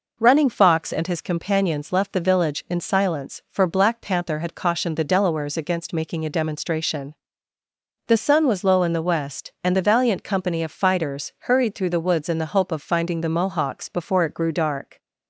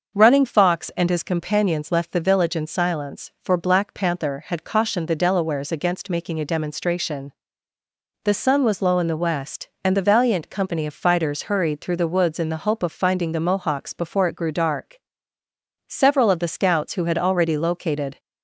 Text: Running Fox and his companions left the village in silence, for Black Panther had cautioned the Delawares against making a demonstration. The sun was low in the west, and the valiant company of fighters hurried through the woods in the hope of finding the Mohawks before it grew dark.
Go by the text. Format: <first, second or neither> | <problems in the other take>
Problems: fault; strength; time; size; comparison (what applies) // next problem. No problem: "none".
first | starts louder than the rest; until 1.2 s; 6 dB // goes on to say "Several of the scouts who had already located"; strong; from 15.8 s on; 2.3 s long